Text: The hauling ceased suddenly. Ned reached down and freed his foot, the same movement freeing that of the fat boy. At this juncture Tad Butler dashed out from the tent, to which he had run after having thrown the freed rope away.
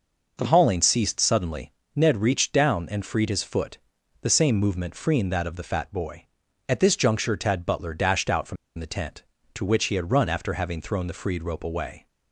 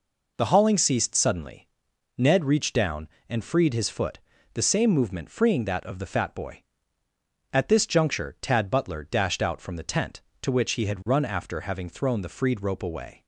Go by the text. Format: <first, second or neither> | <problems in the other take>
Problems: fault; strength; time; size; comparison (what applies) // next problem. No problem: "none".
second | pauses between "from" and "the"; slight; at 8.5 s; 0.23 s long